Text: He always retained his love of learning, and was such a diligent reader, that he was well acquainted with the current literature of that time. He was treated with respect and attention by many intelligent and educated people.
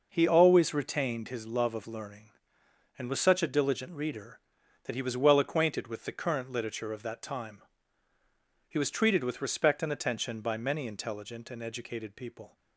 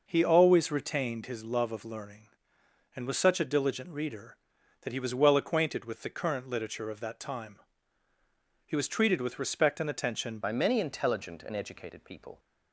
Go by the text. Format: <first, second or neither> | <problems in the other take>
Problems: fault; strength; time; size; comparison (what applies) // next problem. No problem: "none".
first | changes voice at "by"; from 10.4 s on; 1.9 s long